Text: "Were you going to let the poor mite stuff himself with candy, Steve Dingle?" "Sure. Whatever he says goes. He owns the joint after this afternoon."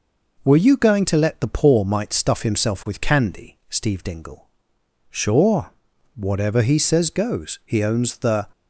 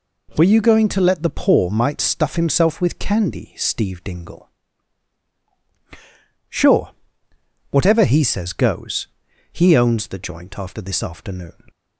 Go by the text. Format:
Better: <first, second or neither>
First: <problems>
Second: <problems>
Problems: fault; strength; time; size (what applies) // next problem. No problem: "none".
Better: second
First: stops before "joint after this afternoon"; at 8.5 s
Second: none